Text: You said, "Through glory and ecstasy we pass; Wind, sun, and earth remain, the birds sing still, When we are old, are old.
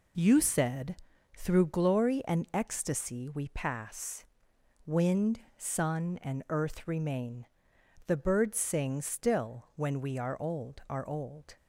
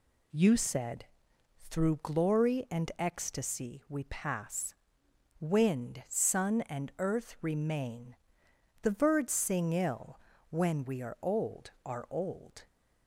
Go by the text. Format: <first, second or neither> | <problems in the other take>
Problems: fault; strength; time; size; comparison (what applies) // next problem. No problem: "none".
first | says "ill" for "still"; at 9.7 s